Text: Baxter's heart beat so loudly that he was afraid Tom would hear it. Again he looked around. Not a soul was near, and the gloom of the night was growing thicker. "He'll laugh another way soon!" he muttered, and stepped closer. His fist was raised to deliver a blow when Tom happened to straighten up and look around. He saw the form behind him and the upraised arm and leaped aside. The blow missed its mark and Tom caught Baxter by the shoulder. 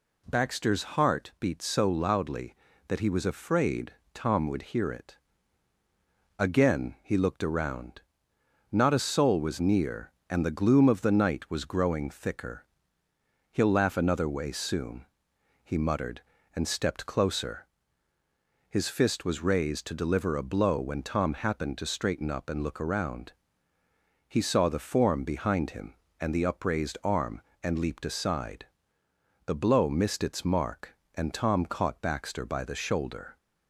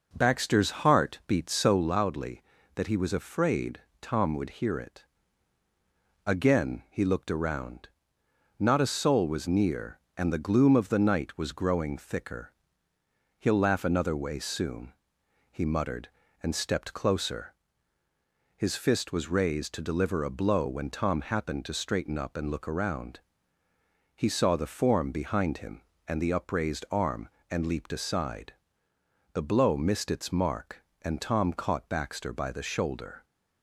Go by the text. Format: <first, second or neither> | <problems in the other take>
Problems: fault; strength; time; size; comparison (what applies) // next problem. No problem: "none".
first | starts louder than the rest; noticeable; until 2.0 s; 5.5 dB // pauses between "afraid" and "Tom"; slight; at 3.7 s; 0.20 s long; slight in the first